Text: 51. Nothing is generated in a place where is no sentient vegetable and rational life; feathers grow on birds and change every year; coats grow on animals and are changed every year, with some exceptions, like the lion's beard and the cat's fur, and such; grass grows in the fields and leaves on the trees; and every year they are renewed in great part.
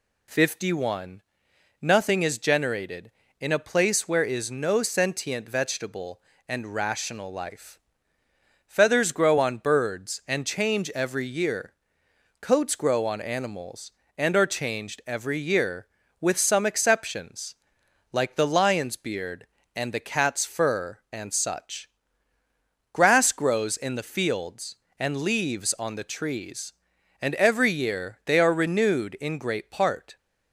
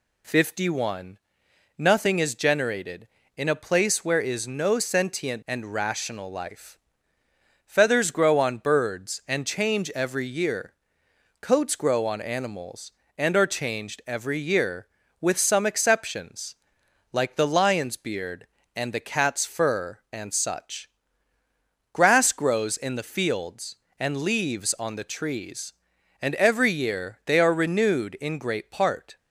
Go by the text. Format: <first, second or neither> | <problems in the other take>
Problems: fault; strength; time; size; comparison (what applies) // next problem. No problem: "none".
first | skips "vegetable"; at 5.4 s